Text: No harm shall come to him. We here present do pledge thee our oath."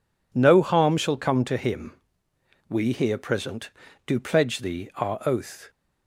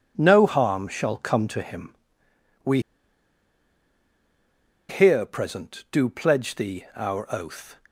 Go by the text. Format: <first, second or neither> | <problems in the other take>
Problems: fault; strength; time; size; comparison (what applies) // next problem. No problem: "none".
first | pauses between "We" and "here"; strong; at 2.7 s; 2.0 s long